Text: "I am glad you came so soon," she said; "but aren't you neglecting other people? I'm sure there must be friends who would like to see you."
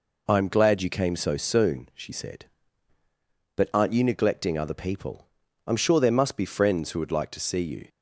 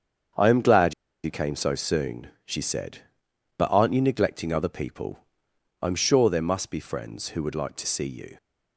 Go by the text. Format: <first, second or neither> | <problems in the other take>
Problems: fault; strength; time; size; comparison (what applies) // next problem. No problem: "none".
first | starts louder than the rest; strong; until 1.6 s; 7.5 dB // pauses between "glad" and "you"; slight; at 0.9 s; 0.31 s long